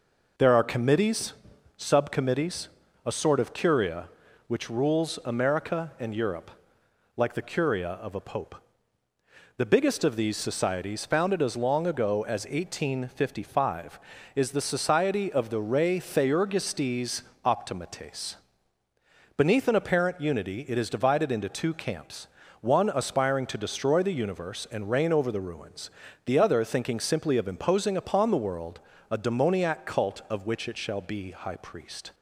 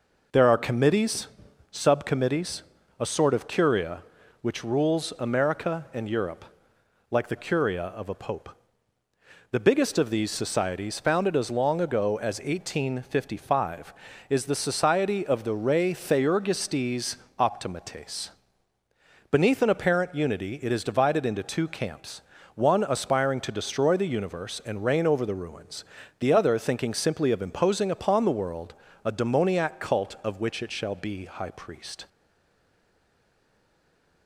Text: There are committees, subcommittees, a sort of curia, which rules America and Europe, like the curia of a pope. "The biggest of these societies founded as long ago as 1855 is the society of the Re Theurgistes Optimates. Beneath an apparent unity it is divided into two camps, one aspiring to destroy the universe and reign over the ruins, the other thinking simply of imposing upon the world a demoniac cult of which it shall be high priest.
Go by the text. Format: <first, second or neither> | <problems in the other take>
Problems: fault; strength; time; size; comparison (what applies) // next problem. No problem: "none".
first | pauses between "Theurgistes" and "Optimates"; slight; at 17.1 s; 0.22 s long; slight in the first // pauses between "world" and "a"; slight; at 28.7 s; 0.30 s long; slight in the first // stays silent after the last word; from 32.0 s on; 2.2 s long